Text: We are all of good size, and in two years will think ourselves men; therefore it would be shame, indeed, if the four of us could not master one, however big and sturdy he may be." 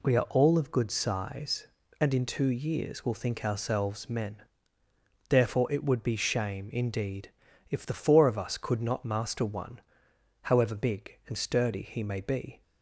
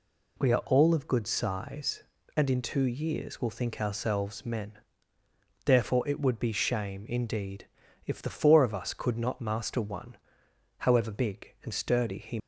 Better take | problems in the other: first | stops before "may be"; at 12.3 s

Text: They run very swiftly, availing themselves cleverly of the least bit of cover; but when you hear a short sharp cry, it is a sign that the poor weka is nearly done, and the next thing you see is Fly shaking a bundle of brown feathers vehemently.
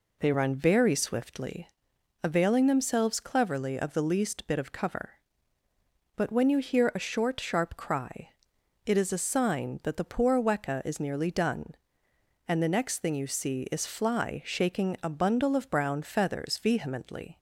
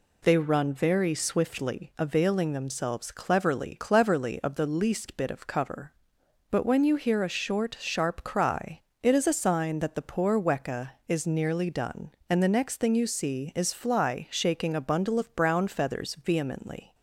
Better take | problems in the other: first | says "cleverly" twice; at 3.7 s

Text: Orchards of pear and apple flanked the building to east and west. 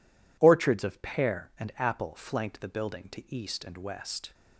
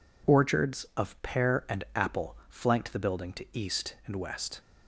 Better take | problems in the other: neither | none

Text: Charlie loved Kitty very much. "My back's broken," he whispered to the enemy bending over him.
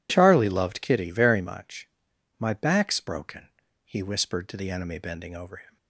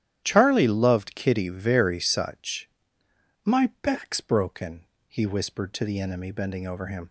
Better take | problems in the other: first | starts louder than the rest; strong; until 1.2 s; 11 dB // says "such" for "much"; at 1.9 s

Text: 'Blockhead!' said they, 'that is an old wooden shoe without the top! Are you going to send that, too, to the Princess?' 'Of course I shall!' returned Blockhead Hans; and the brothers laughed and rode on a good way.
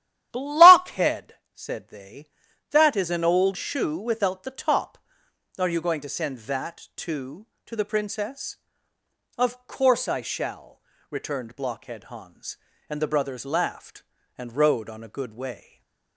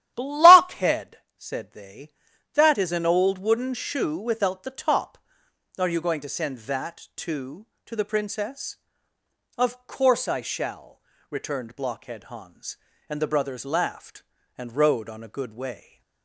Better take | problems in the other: second | starts louder than the rest; strong; until 1.3 s; 12 dB; strong in the second // skips "wooden"; at 3.5 s // stays silent after the last word; slight; from 15.6 s on; 0.5 s long

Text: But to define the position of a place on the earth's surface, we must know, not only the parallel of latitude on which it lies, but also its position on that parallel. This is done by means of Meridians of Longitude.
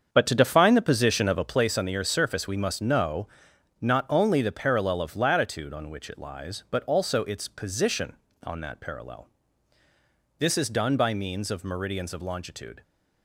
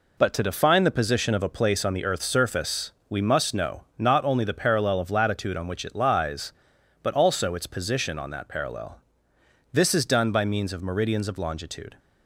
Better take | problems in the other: second | starts louder than the rest; strong; until 1.8 s; 7 dB

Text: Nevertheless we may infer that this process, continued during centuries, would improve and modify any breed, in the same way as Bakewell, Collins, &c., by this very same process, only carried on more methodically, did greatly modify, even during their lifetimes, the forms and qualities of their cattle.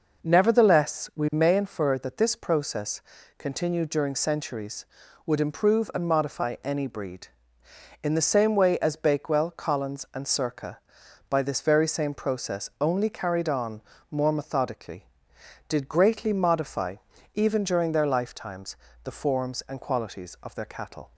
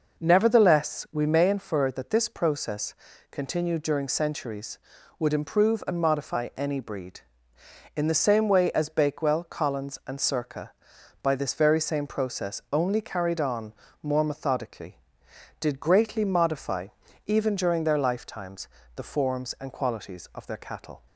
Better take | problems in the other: neither | pauses between "on" and "more"; slight; the same in both

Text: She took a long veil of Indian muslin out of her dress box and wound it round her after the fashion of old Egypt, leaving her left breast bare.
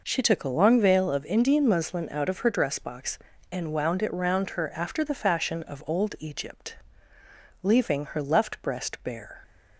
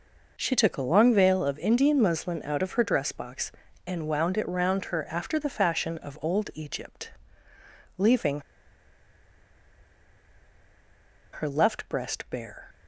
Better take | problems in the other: first | pauses between "leaving" and "her"; strong; at 8.4 s; 2.9 s long

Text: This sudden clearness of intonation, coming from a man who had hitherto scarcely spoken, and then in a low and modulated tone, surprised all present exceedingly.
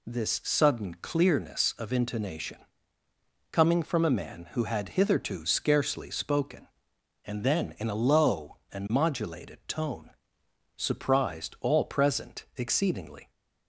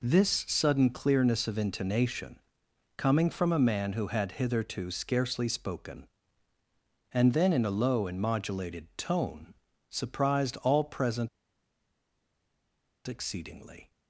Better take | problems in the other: first | pauses between "present" and "exceedingly"; strong; at 11.2 s; 1.7 s long

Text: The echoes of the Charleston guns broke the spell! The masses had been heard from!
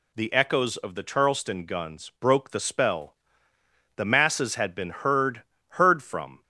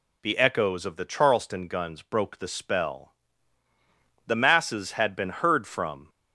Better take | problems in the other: second | says "heard" twice; at 5.6 s

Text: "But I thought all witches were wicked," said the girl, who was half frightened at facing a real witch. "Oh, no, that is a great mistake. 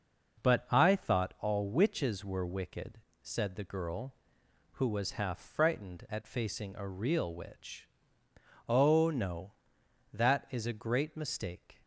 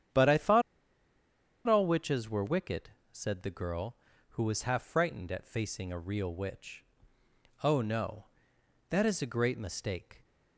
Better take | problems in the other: first | starts louder than the rest; strong; until 2.1 s; 9 dB // pauses between "thought" and "all"; at 0.6 s; 1.0 s long

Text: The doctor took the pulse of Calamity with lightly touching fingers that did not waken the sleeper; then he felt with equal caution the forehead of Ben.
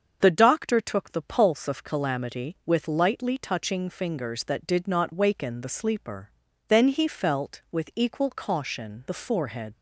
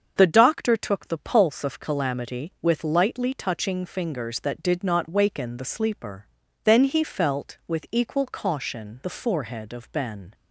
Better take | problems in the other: second | starts louder than the rest; until 1.2 s; 7 dB; also in the second // stops before "of Ben"; at 9.7 s

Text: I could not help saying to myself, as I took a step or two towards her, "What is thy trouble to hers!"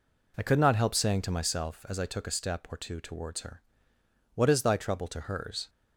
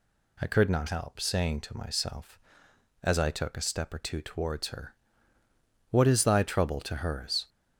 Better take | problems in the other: neither | none

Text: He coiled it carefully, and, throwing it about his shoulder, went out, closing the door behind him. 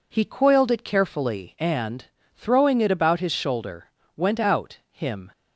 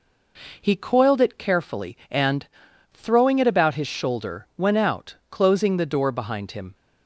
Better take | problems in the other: second | skips "closing the door behind"; at 4.8 s

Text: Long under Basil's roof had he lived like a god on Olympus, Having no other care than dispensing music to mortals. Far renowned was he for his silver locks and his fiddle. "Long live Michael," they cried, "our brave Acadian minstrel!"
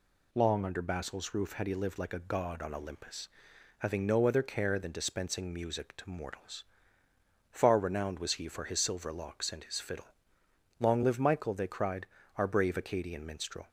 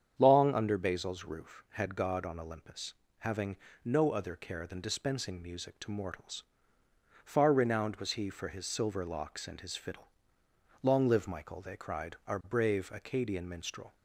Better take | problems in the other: first | starts louder than the rest; strong; until 1.1 s; 8 dB // skips "he lived like a"; at 1.9 s // pauses between "Having" and "no"; slight; at 3.5 s; 0.28 s long

